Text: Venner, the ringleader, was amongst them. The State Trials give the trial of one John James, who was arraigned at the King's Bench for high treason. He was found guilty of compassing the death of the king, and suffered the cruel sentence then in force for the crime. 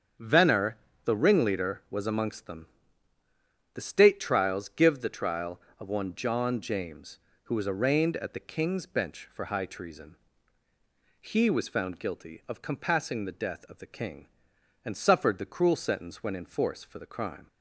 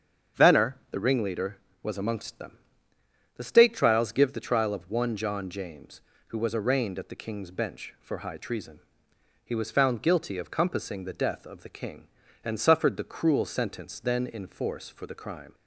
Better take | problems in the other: second | starts louder than the rest; strong; until 1.4 s; 7.5 dB; strong in the second // says "when" for "then"; at 16.2 s

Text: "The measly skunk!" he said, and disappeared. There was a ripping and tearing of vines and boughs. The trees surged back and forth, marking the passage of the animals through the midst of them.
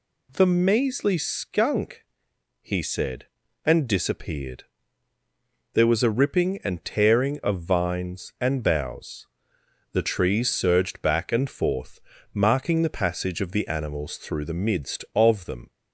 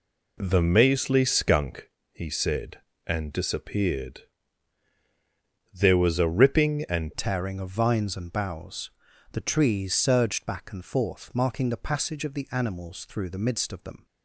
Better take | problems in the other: first | changes voice at "tearing"; from 7.1 s on; 6.9 s long

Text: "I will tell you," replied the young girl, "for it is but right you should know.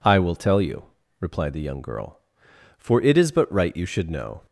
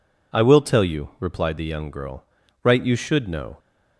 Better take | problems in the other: first | skips "for it is but"; at 2.4 s

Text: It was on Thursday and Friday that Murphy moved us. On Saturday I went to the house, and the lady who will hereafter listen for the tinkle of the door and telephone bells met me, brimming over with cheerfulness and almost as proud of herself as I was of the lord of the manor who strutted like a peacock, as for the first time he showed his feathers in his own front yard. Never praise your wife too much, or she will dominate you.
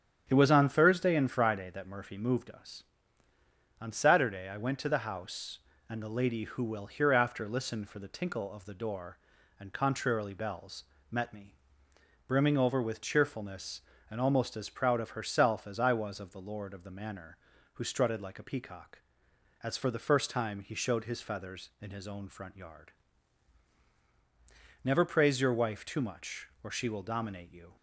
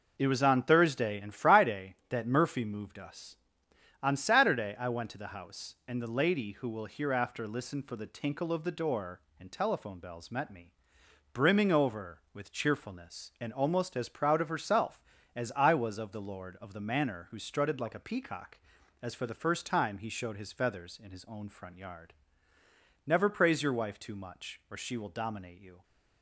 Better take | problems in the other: second | starts louder than the rest; strong; until 1.3 s; 8.5 dB // says "contrarily" for "telephone"; at 9.7 s // pauses between "bells" and "met"; slight; at 10.8 s; 0.30 s long

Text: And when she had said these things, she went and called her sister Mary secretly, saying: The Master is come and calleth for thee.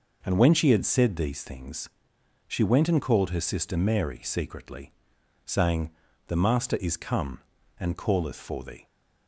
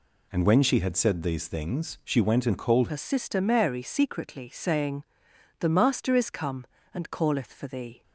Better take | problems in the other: first | changes voice at "her"; from 2.8 s on; 5.2 s long

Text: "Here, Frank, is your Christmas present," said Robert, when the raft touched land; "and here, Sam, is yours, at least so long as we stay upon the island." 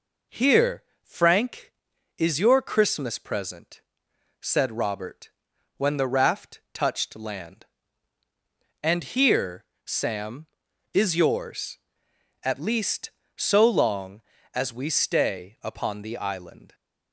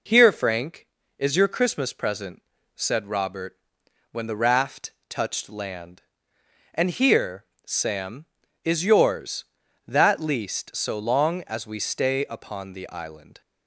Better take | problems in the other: first | pauses between "raft" and "touched"; slight; at 4.9 s; 0.16 s long // says "that" for "at"; at 9.8 s

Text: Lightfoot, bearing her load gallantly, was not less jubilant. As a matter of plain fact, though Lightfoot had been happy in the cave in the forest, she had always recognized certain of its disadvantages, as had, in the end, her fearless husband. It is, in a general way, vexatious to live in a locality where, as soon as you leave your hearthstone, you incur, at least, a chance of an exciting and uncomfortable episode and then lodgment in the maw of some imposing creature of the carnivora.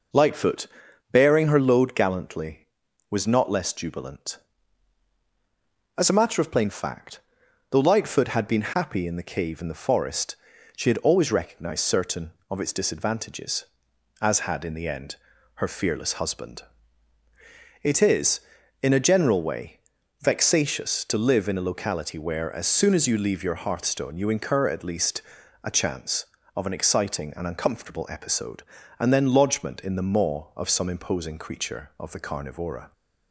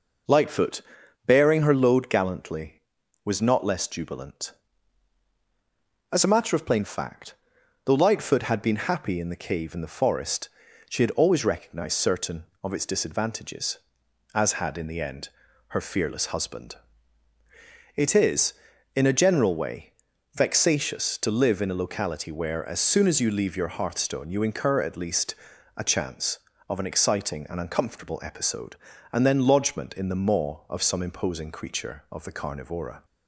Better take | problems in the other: neither | none

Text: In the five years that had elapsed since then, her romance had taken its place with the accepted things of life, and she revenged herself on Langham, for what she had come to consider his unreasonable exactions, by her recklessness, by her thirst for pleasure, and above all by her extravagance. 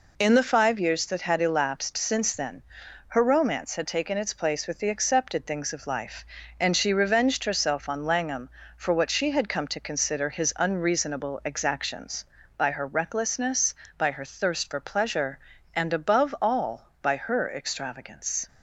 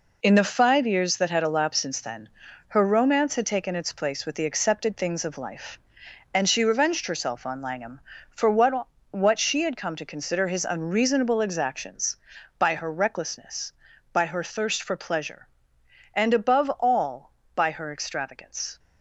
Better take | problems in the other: first | says "what" twice; at 9.0 s

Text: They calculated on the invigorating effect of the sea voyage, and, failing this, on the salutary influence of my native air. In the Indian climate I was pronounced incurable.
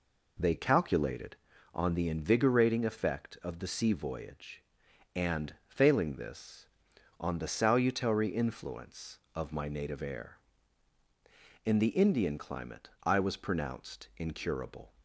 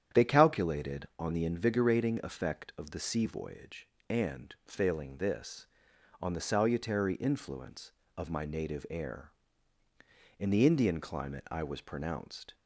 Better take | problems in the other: first | starts louder than the rest; strong; until 1.2 s; 9.5 dB // stops before "incurable"; at 12.5 s

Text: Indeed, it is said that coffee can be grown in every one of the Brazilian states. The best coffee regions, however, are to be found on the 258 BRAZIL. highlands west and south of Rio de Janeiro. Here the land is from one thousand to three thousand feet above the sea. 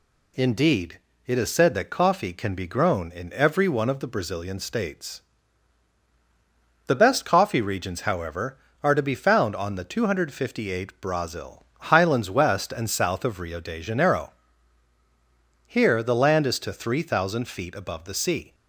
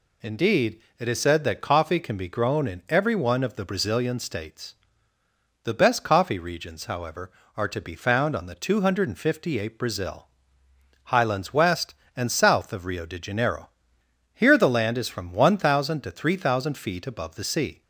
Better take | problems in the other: second | skips "from one thousand"; at 16.5 s

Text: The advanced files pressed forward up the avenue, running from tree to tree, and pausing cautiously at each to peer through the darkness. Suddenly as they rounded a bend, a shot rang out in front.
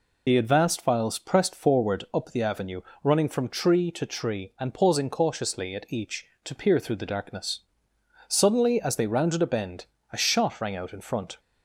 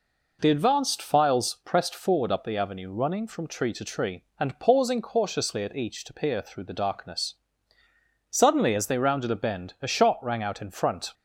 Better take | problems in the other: second | loses the start of "The"; at 0.2 s; 40 ms

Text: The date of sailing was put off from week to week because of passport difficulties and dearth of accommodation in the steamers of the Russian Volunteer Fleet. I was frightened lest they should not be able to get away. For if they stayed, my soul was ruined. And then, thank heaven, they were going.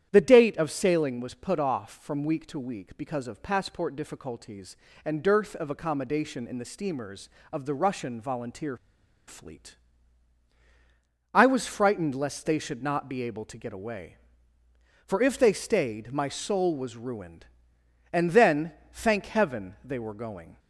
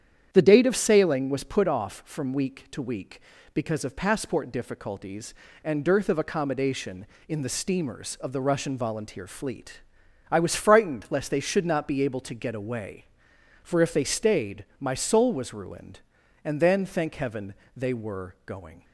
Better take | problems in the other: second | starts louder than the rest; strong; until 1.1 s; 10 dB; strong in the second // pauses between "Volunteer" and "Fleet"; noticeable; at 8.7 s; 0.52 s long

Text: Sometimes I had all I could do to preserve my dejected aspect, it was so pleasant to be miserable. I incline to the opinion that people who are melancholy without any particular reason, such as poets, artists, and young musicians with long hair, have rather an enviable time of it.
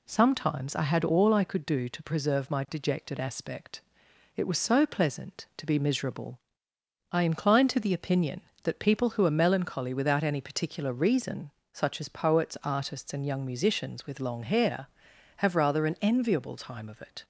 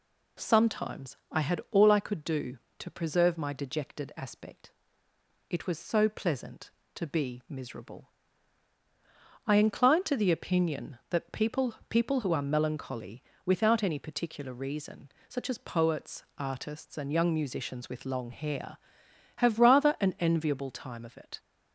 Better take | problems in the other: first | pauses between "Sometimes" and "I"; slight; at 1.1 s; 0.16 s long // says "people" twice; at 11.8 s // pauses between "melancholy" and "without"; slight; at 13.2 s; 0.22 s long

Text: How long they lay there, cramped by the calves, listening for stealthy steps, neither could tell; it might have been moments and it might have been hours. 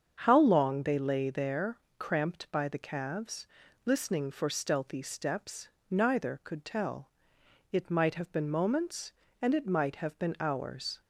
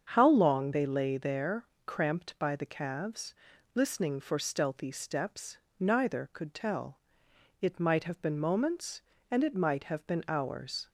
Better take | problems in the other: neither | starts louder than the rest; strong; the same in both

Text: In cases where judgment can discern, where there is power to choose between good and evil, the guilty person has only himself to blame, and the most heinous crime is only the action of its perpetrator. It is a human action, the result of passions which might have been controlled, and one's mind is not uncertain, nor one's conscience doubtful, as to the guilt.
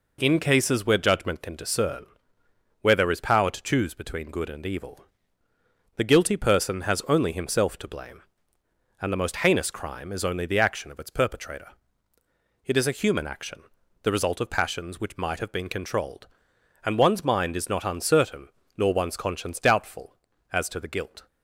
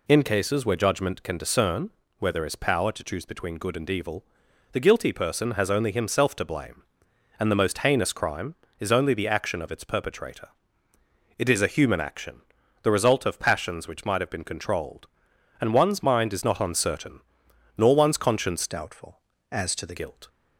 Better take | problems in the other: first | changes voice from "doubtful" to "the"; from 18.6 to 19.9 s; 1.3 s long

